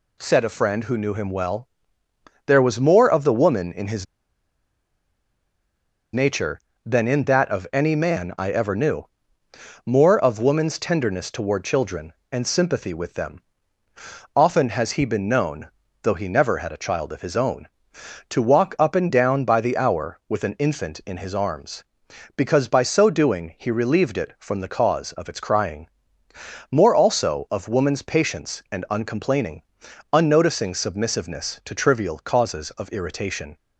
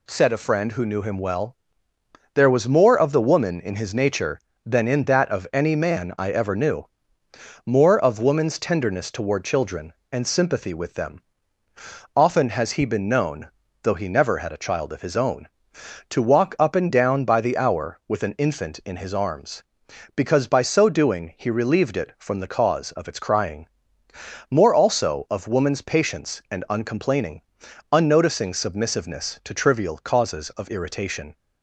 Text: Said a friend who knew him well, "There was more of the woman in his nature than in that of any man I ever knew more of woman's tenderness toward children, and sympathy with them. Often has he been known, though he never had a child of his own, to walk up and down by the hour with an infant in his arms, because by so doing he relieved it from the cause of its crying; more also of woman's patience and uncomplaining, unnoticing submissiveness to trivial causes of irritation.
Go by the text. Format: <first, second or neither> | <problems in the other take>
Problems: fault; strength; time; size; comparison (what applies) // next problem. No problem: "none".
second | pauses between "his" and "nature"; strong; at 4.0 s; 2.0 s long // pauses between "knew" and "more"; noticeable; at 9.0 s; 0.78 s long; noticeable in the second